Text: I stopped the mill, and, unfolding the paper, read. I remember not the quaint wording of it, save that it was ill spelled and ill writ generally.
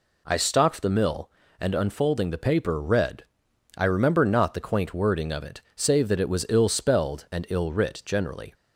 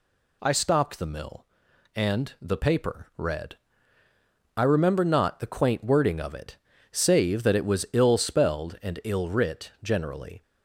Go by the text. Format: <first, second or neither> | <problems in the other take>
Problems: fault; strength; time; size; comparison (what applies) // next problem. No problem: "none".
first | skips "unfolding"; at 2.3 s